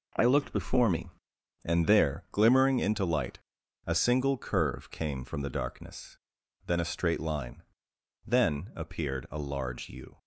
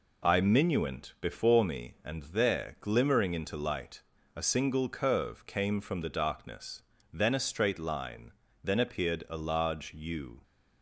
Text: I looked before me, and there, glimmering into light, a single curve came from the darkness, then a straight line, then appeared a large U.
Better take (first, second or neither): first